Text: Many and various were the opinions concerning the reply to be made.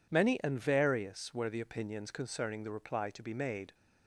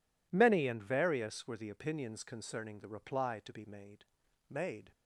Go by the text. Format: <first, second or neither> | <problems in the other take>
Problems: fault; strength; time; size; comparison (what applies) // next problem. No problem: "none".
first | says "made" twice; at 4.4 s